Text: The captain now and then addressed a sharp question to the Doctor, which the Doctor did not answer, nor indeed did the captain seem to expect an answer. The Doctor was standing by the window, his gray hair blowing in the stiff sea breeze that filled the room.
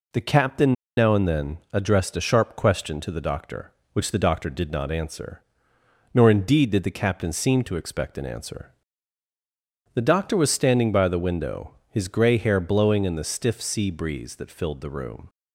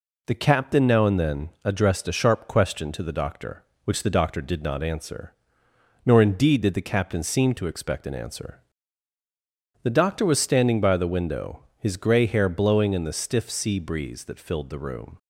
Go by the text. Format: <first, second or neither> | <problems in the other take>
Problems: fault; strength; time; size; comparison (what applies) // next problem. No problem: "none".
second | pauses between "captain" and "now"; slight; at 0.7 s; 0.24 s long // pauses between "then" and "addressed"; slight; at 1.5 s; 0.16 s long; slight in the second